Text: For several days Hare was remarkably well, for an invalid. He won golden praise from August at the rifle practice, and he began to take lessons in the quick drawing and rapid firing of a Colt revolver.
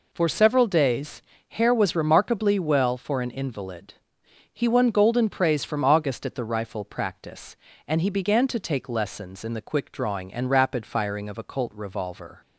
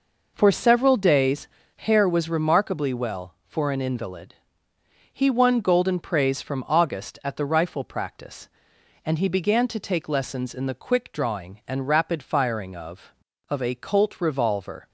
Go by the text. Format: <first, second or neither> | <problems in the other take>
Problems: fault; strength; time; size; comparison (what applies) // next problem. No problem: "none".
first | pauses between "days" and "Hare"; slight; at 1.4 s; 0.30 s long; slight in the first // says "of" twice; at 13.4 s